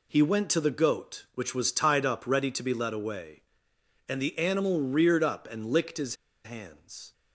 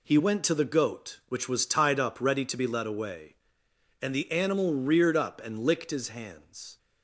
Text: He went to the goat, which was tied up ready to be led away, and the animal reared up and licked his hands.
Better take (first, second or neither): second